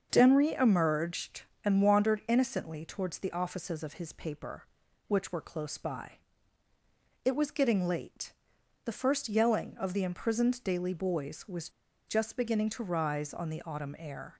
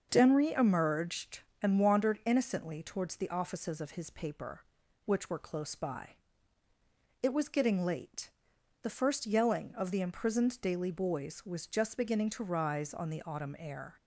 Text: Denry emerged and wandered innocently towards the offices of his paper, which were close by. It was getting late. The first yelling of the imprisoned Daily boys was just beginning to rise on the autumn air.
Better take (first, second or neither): second